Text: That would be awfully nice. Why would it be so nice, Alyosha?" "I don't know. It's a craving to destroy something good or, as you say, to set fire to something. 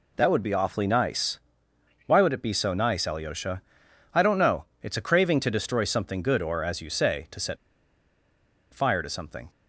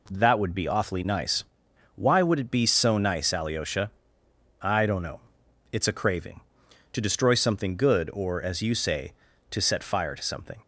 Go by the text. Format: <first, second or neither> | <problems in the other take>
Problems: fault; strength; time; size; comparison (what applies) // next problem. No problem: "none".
second | pauses between "set" and "fire"; at 7.5 s; 1.1 s long